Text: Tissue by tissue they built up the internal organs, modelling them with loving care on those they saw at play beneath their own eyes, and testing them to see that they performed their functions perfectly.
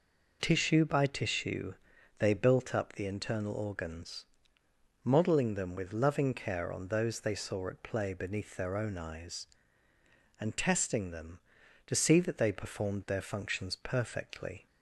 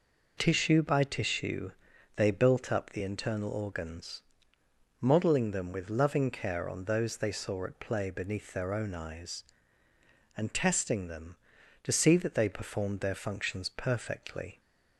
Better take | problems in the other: neither | pauses between "tissue" and "they"; the same in both

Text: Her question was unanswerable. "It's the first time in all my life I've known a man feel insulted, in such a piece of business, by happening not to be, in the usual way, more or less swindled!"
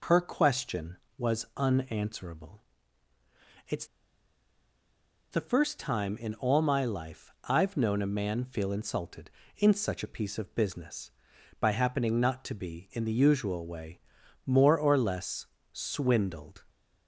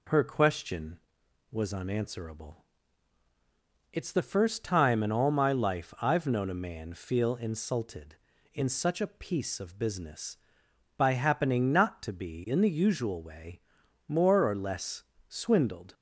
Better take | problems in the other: second | pauses between "It's" and "the"; strong; at 3.8 s; 1.4 s long // pauses between "less" and "swindled"; slight; at 15.4 s; 0.26 s long; slight in the second

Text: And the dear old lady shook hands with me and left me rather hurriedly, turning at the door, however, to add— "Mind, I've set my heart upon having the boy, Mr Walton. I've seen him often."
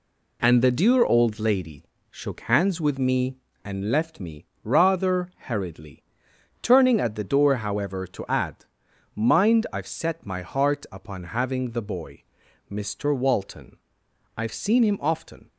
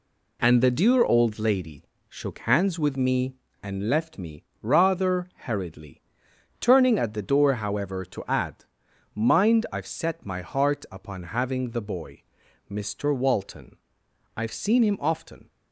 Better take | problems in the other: neither | pauses between "lady" and "shook"; slight; the same in both // pauses between "me" and "rather"; slight; the same in both // pauses between "rather" and "hurriedly"; slight; the same in both

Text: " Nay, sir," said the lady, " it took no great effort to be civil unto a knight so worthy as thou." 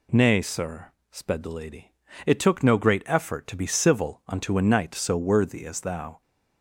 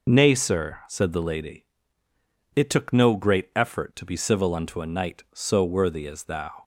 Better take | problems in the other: second | says "sped" for "said"; at 1.1 s

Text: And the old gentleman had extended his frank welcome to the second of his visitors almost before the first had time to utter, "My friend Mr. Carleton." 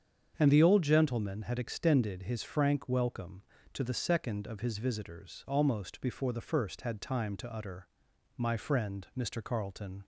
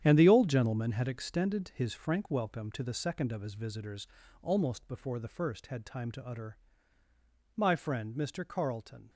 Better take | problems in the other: first | gets quieter; strong; throughout; 11 dB // starts louder than the rest; strong; until 1.0 s; 9.5 dB; strong in the first // pauses between "visitors" and "almost"; slight; at 4.0 s; 0.36 s long

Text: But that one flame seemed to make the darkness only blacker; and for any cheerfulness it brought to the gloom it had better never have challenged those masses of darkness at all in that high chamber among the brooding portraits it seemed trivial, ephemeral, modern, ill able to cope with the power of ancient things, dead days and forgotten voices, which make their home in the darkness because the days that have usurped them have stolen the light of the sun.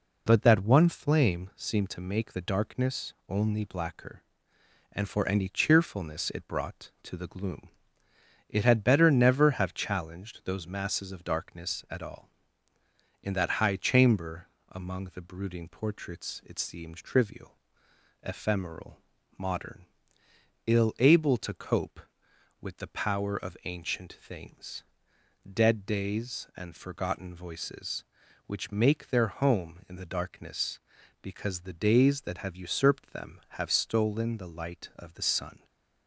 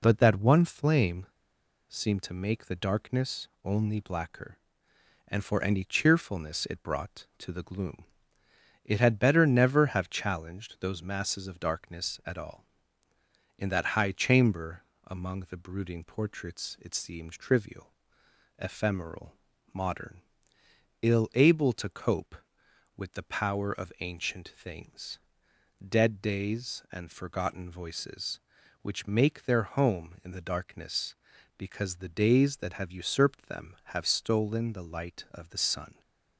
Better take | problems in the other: first | pauses between "flame" and "seemed"; noticeable; at 1.2 s; 0.61 s long // pauses between "darkness" and "only"; slight; at 3.4 s; 0.16 s long // pauses between "gloom" and "it"; noticeable; at 8.0 s; 0.80 s long; noticeable in the first // pauses between "chamber" and "among"; slight; at 14.8 s; 0.24 s long; slight in the first

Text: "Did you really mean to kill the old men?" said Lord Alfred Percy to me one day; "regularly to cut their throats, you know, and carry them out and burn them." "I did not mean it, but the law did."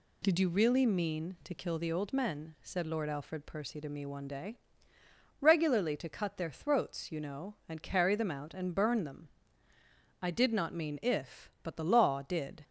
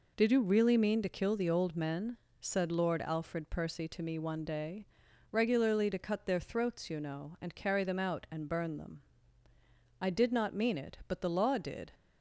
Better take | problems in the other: second | says "if" for "it"; at 11.0 s

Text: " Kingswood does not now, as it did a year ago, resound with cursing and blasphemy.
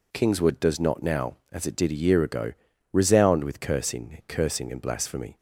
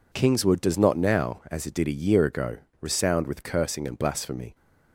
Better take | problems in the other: second | says "cursing" twice; at 4.2 s

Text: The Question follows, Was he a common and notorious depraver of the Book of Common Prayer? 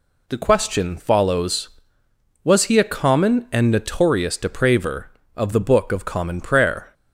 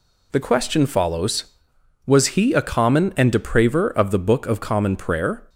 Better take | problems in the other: first | skips "notorious"; at 3.3 s

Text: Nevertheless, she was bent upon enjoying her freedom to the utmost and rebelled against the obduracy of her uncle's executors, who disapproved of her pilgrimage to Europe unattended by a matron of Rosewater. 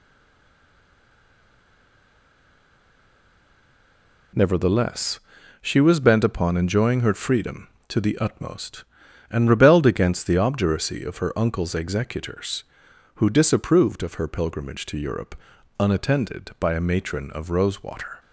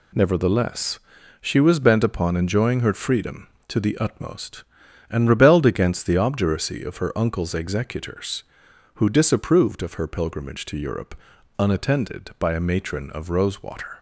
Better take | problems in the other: second | stays silent before the first word; strong; until 4.3 s; 4.3 s long // pauses between "Europe" and "unattended"; at 15.3 s; 0.44 s long; also in the second

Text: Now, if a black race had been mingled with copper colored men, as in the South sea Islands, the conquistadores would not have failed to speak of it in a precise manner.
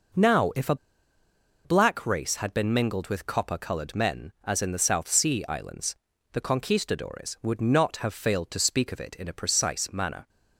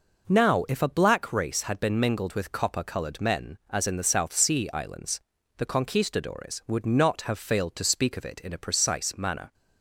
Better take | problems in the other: second | pauses between "a" and "black"; noticeable; at 0.7 s; 0.88 s long

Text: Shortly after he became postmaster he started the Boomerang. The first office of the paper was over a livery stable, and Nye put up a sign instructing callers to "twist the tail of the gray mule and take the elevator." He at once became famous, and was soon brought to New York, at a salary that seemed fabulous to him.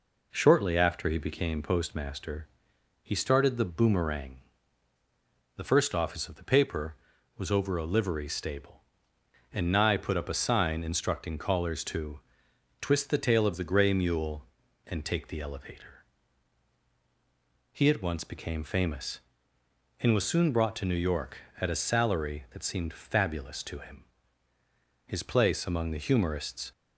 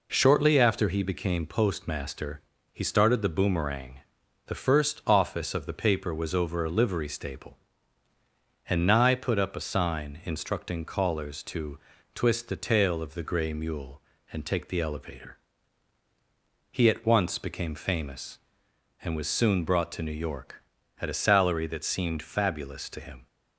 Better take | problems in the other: second | pauses between "postmaster" and "he"; noticeable; at 2.4 s; 0.56 s long; slight in the second // pauses between "to" and "twist"; noticeable; at 12.2 s; 0.58 s long; slight in the second // goes on to say "His place among the humorists"; from 25.0 s on; 1.6 s long

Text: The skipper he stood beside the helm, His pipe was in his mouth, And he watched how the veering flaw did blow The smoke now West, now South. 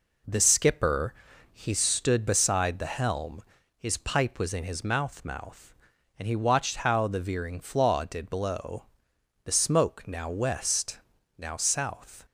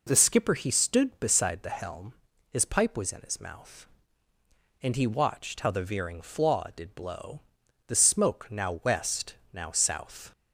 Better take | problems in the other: second | pauses between "skipper" and "he"; at 1.1 s; 0.40 s long // says "mouth" twice; at 5.2 s // pauses between "blow" and "The"; noticeable; at 8.8 s; 0.60 s long; noticeable in the second

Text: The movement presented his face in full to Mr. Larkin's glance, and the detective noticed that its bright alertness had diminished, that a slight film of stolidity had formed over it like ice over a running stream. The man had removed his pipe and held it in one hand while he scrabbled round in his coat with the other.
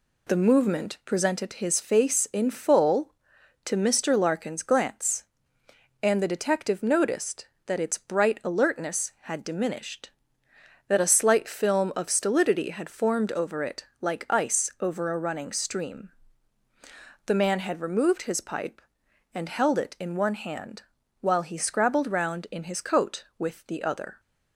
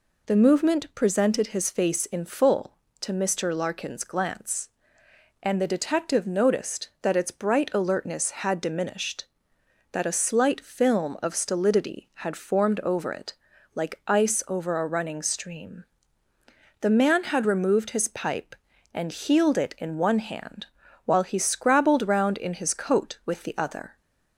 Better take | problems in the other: first | pauses between "it" and "like"; at 13.3 s; 0.40 s long // says "healed" for "held"; at 19.1 s // pauses between "hand" and "while"; at 20.6 s; 0.40 s long; also in the first

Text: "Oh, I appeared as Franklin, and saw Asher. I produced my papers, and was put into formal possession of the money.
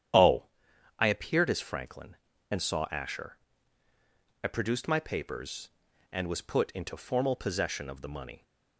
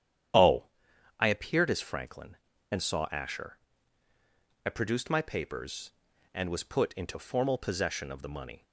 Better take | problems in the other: neither | starts louder than the rest; strong; the same in both

